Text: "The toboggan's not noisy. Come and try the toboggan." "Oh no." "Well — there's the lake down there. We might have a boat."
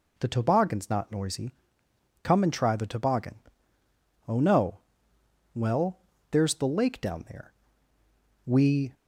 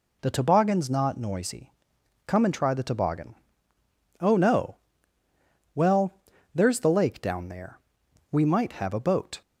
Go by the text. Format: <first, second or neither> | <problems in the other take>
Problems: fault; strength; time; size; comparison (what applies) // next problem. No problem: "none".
second | stops before "might have a boat"; at 8.9 s